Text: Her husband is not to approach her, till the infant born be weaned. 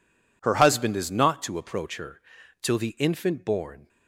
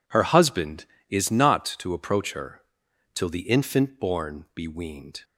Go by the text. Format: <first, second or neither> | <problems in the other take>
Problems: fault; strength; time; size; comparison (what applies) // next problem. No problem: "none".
second | stops before "be weaned"; at 3.8 s